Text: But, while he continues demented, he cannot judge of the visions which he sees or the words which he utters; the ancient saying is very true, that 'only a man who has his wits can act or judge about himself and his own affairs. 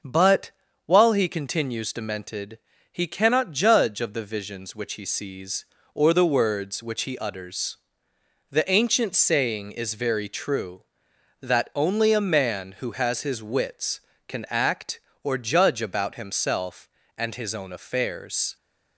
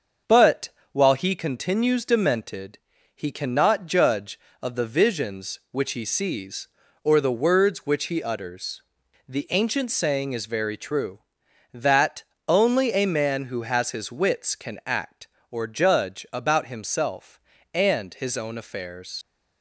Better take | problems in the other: first | starts louder than the rest; until 1.4 s; 6.5 dB; also in the first // pauses between "that" and "only"; slight; at 12.2 s; 0.24 s long // leaves "affairs" unfinished; at 19.2 s; 85 ms

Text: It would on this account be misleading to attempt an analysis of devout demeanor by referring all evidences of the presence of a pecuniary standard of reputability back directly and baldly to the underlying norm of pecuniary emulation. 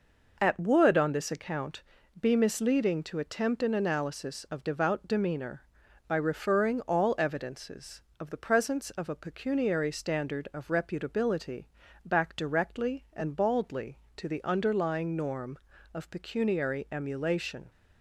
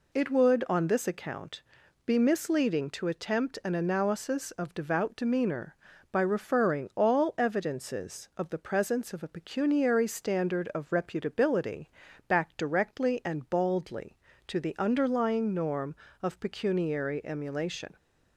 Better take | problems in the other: second | says "At" for "It"; at 0.3 s // pauses between "account" and "be"; at 1.8 s; 0.38 s long; also in the second // pauses between "reputability" and "back"; at 11.6 s; 0.40 s long; also in the second

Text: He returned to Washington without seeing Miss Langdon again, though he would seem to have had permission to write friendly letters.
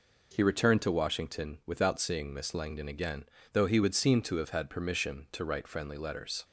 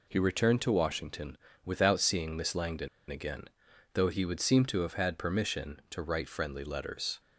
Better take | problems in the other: first | pauses between "Washington" and "without"; slight; at 1.3 s; 0.28 s long // pauses between "Langdon" and "again"; slight; at 2.8 s; 0.21 s long

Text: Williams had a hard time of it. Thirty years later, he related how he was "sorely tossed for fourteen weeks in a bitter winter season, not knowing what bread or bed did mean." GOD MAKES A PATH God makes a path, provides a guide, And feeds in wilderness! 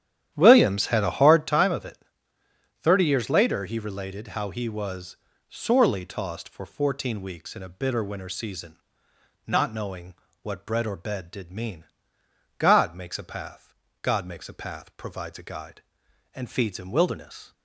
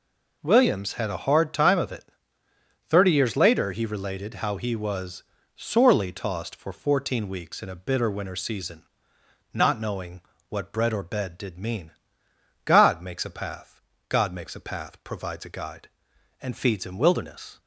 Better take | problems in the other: second | starts louder than the rest; strong; until 1.6 s; 11 dB // pauses between "was" and "sorely"; slight; at 5.1 s; 0.32 s long; slight in the second // pauses between "knowing" and "what"; slight; at 10.1 s; 0.26 s long; slight in the second // pauses between "PATH" and "God"; slight; at 13.7 s; 0.26 s long; slight in the second

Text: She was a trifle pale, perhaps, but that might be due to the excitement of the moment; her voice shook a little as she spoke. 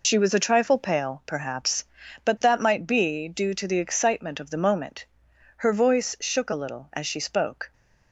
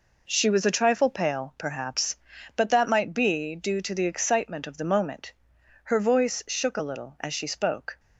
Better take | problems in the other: second | loses the start of "She"; at 0.0 s; 90 ms

